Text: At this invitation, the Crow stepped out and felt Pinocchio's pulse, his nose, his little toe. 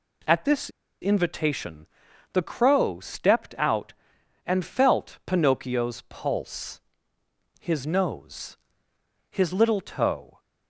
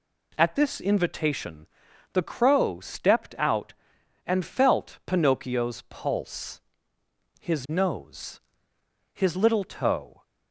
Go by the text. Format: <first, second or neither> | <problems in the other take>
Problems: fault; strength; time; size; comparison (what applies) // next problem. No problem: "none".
second | pauses between "this" and "invitation"; slight; at 0.7 s; 0.31 s long